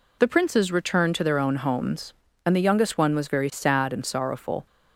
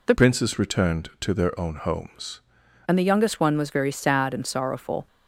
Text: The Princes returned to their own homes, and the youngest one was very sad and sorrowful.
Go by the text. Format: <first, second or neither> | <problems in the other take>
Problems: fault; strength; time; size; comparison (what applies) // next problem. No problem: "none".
first | changes voice from "Princes" to "homes"; from 0.1 to 2.4 s; 2.3 s long